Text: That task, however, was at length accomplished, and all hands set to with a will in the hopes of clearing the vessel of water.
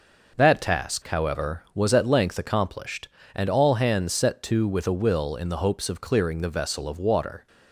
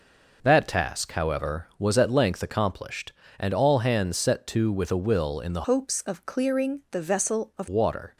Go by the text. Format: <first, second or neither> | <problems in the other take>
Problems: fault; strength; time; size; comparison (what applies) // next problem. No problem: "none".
first | changes voice from "hopes" to "of"; from 5.6 to 7.6 s; 2.0 s long